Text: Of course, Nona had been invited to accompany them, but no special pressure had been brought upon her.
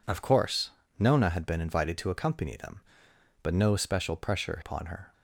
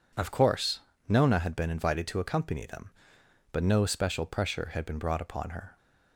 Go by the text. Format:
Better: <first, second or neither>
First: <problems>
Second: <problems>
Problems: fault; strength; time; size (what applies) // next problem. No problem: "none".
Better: second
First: skips "had been brought"; at 4.6 s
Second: none